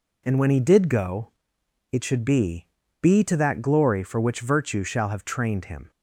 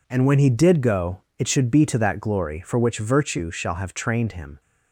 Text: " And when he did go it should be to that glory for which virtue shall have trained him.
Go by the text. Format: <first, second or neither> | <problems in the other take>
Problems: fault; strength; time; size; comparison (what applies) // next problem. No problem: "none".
second | pauses between "go" and "it"; noticeable; at 1.3 s; 0.60 s long; slight in the second // says "be" twice; at 3.0 s